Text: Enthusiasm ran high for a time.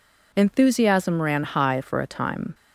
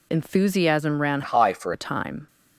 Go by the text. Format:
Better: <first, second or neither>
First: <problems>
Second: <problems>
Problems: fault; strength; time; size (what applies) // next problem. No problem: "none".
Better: first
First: none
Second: changes voice from "high" to "for"; from 1.2 to 1.7 s; 0.5 s long